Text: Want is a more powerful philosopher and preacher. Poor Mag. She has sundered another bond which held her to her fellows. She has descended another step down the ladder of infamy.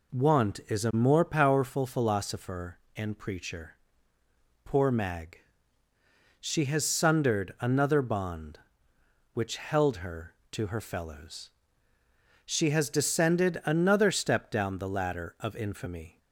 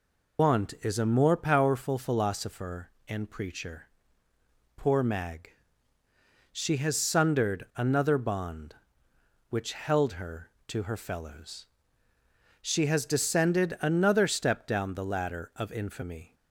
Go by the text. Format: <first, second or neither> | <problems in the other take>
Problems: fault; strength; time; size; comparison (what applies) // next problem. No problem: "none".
first | loses the start of "Want"; at 0.3 s; 135 ms